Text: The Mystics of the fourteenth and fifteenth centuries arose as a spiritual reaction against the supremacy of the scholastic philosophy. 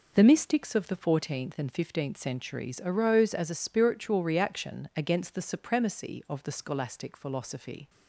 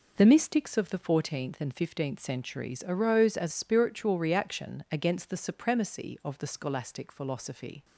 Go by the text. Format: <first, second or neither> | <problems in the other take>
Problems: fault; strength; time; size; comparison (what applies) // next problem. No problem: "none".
first | skips "a"; at 3.5 s